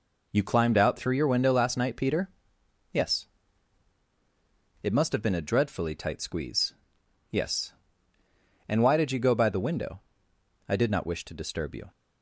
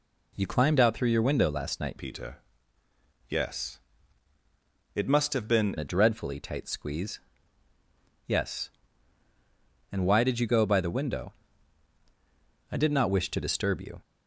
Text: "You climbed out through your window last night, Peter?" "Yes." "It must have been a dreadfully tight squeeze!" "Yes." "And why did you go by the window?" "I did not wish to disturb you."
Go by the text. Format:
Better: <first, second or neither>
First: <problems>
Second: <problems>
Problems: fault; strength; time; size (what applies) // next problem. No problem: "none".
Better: first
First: none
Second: changes voice from "Peter" to "been"; from 1.9 to 5.7 s; 3.8 s long